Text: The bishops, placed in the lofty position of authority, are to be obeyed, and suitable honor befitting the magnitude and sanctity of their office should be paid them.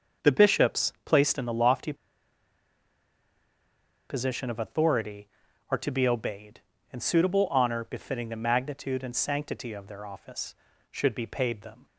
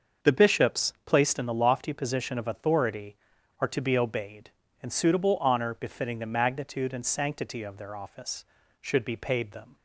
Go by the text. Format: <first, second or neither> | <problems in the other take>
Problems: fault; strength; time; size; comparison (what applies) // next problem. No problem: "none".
second | starts louder than the rest; until 1.3 s; 6.5 dB; also in the second // pauses between "lofty" and "position"; strong; at 1.9 s; 2.1 s long